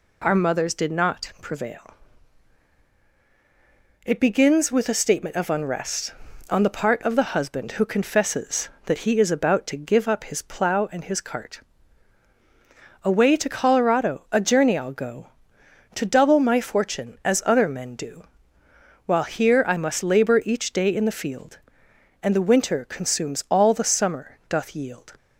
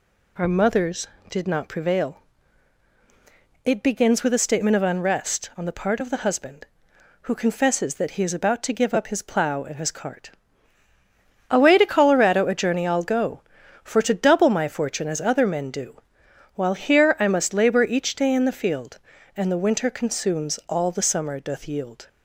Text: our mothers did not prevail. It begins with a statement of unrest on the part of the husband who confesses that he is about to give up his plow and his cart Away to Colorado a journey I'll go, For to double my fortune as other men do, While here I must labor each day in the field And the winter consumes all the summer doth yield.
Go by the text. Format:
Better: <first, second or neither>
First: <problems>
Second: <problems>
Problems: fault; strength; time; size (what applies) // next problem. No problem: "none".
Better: second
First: pauses between "cart" and "Away"; strong; at 11.6 s; 1.4 s long // skips "For"; at 15.6 s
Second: pauses between "cart" and "Away"; at 10.2 s; 1.1 s long